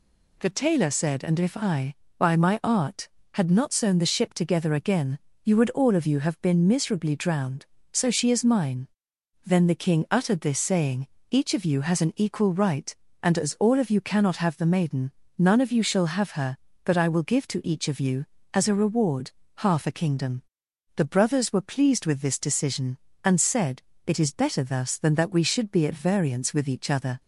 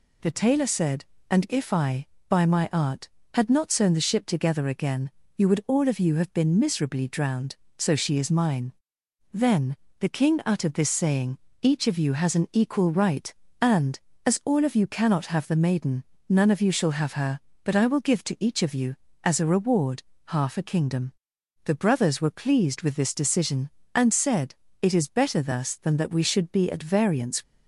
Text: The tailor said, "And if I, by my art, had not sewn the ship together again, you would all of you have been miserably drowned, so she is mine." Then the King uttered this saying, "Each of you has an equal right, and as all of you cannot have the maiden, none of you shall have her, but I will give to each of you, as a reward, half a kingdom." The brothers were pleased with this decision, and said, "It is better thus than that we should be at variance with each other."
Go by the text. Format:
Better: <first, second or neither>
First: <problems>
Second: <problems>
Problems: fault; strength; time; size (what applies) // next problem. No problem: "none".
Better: first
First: none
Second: pauses between "Then" and "the"; slight; at 9.7 s; 0.24 s long // stops before "with each other"; at 27.4 s